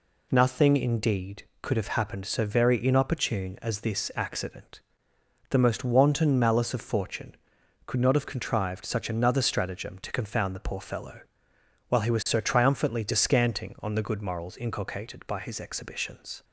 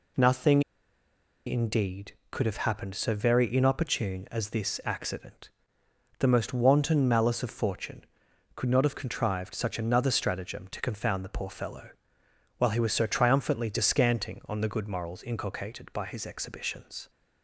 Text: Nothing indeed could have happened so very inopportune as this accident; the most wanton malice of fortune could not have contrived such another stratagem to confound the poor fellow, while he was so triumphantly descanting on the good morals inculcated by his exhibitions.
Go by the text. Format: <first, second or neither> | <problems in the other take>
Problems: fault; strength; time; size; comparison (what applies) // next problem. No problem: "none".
first | pauses between "Nothing" and "indeed"; noticeable; at 0.6 s; 0.86 s long